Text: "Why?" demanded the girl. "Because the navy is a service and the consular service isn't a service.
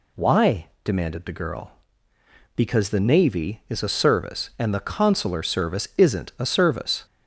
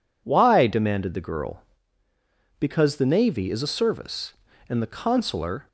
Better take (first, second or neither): first